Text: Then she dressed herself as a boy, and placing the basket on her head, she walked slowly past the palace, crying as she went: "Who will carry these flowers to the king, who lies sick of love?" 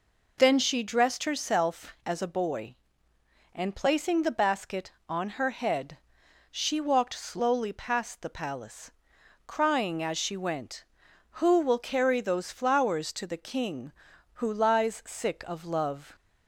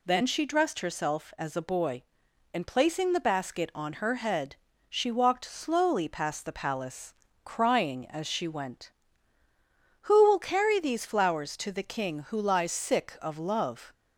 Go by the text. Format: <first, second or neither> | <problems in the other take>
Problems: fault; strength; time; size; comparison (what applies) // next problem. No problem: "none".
second | says "those" for "these"; at 12.2 s